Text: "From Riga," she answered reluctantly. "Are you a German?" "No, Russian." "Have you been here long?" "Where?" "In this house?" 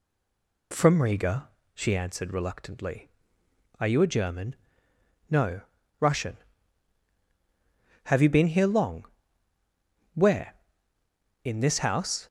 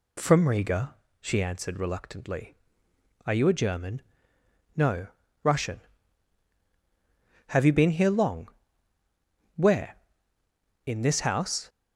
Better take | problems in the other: second | stays silent before the first word; slight; until 0.7 s; 0.7 s long

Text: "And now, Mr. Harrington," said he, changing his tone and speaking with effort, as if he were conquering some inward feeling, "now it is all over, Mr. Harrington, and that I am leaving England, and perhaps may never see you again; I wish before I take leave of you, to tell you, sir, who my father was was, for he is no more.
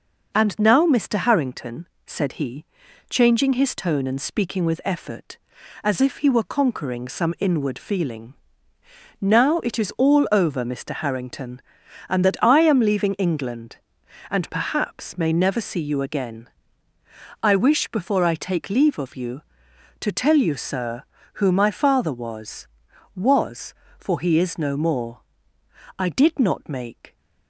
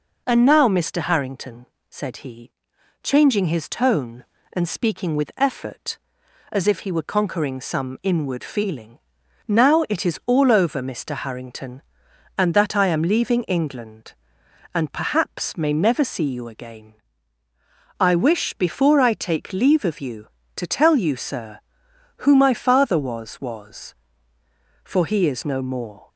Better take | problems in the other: second | goes on to say "I did not make"; noticeable; from 25.9 s on; 1.2 s long

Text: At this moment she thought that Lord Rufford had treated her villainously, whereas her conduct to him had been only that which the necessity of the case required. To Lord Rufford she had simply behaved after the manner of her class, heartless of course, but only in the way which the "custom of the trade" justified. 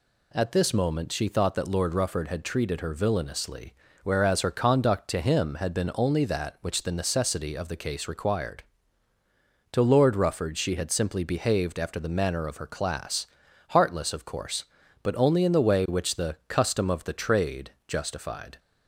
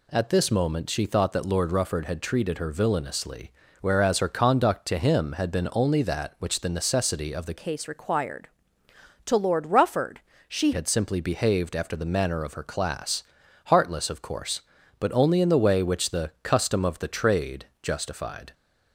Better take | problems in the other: first | changes voice from "case" to "she"; from 7.5 to 10.7 s; 3.2 s long // pauses between "Rufford" and "she"; slight; at 10.1 s; 0.28 s long // pauses between "trade" and "justified"; slight; at 17.6 s; 0.16 s long; slight in the first

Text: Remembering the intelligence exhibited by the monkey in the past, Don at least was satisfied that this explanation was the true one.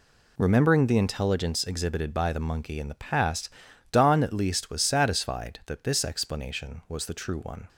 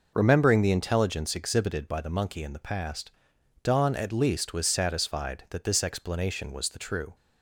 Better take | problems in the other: first | stops before "one"; at 7.1 s

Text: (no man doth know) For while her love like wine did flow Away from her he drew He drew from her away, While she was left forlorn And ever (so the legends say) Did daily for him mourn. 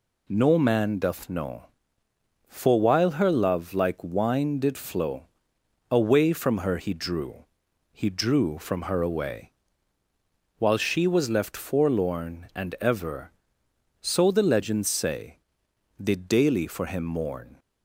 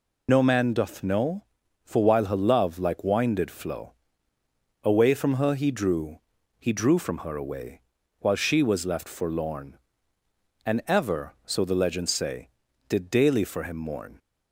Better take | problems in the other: first | loses the start of "no"; at 0.2 s; 55 ms // pauses between "flow" and "Away"; noticeable; at 3.9 s; 0.90 s long; noticeable in the first // pauses between "drew" and "He"; at 6.1 s; 0.40 s long; noticeable in the first

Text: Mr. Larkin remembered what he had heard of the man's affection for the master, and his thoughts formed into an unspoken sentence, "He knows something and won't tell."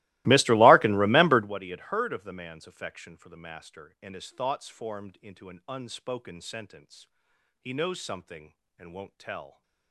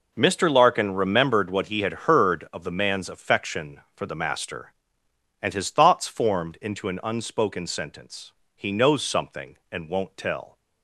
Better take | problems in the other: second | starts louder than the rest; strong; until 1.6 s; 19.5 dB

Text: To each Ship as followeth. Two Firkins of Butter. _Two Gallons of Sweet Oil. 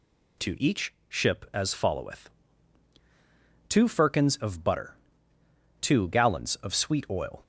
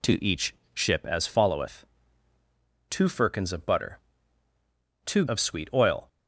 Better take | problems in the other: first | pauses between "each" and "Ship"; slight; at 0.5 s; 0.18 s long; slight in the first // skips "Gallons"; at 5.2 s

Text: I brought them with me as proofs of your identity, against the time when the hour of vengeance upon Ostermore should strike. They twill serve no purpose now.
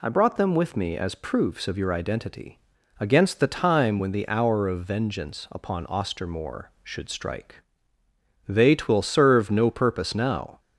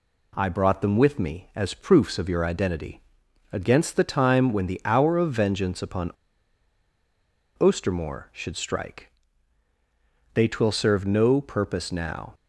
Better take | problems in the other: first | pauses between "upon" and "Ostermore"; strong; at 6.0 s; 1.4 s long

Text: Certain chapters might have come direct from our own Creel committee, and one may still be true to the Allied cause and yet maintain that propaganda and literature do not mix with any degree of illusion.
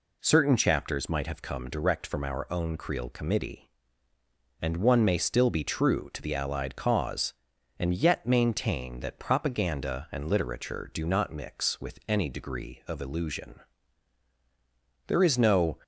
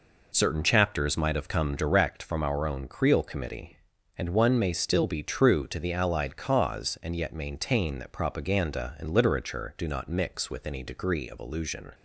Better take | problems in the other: second | goes on to say "There is no"; noticeable; from 15.0 s on; 0.70 s long

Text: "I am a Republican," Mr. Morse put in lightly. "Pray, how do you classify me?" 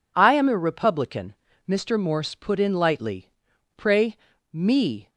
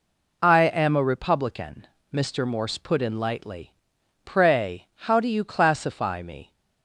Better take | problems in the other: second | skips "how do you classify"; at 4.3 s

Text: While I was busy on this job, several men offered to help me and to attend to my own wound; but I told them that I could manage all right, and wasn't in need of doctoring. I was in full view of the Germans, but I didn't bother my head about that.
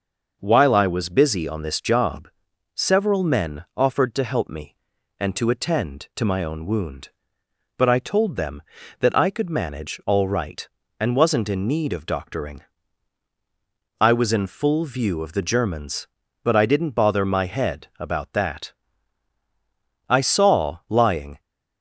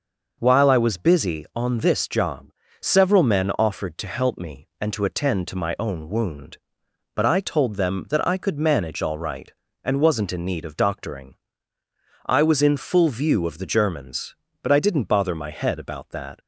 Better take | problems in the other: second | goes on to say "I saw lying"; from 20.0 s on; 1.3 s long

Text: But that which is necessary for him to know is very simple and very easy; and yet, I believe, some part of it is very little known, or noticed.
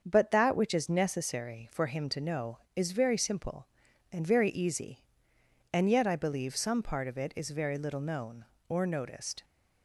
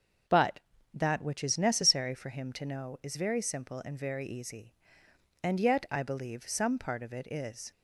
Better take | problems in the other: first | starts louder than the rest; until 1.6 s; 6.5 dB; also in the first // stops before "very little known or noticed"; at 7.7 s

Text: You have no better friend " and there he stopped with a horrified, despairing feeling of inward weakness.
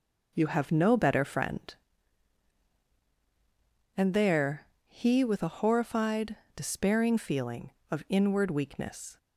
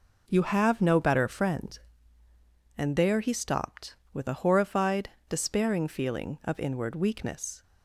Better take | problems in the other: second | pauses between "there" and "he"; slight; at 4.6 s; 0.22 s long // skips "stopped"; at 5.2 s

